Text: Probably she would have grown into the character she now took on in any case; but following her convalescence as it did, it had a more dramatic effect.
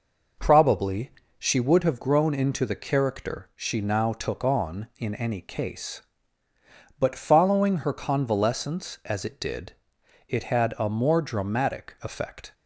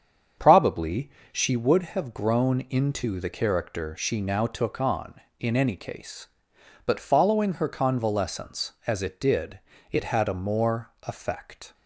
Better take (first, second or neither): first